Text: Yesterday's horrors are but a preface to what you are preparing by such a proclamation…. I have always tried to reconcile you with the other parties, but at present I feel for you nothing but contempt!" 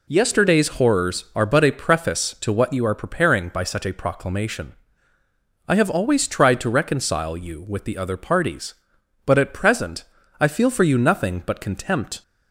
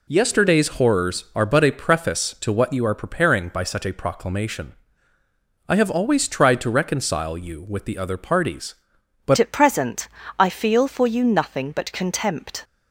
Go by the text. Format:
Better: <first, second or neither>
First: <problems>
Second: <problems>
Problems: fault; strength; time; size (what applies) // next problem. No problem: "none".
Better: first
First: pauses between "present" and "I"; slight; at 10.0 s; 0.36 s long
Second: changes voice at "at"; from 9.3 s on; 3.3 s long // pauses between "present" and "I"; slight; at 10.0 s; 0.32 s long